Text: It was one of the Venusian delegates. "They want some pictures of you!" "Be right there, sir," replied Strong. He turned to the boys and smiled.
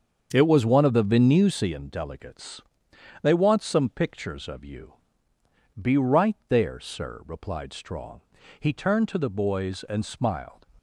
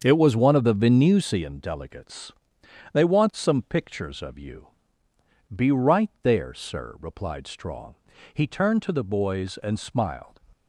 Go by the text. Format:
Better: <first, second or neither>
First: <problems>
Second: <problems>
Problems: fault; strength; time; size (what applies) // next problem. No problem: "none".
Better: neither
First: starts louder than the rest; until 1.3 s; 7 dB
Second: starts louder than the rest; until 1.0 s; 7 dB